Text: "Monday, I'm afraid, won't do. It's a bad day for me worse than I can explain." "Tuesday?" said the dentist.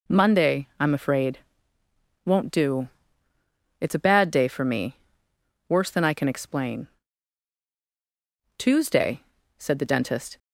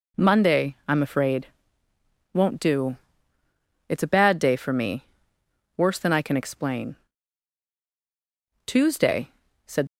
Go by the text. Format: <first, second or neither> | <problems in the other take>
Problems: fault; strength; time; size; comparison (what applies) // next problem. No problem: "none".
first | pauses between "me" and "worse"; noticeable; at 5.0 s; 0.72 s long; noticeable in the first // stops before "the dentist"; at 9.8 s